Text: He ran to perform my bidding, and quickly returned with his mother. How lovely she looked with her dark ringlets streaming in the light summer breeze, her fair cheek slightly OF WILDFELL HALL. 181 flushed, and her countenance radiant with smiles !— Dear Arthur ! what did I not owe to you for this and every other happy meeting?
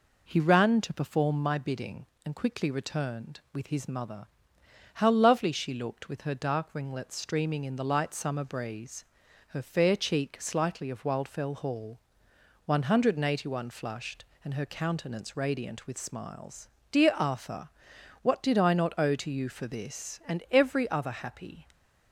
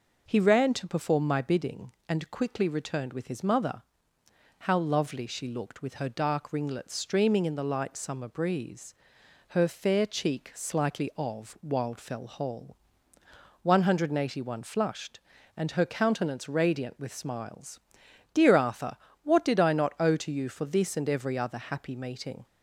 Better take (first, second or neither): second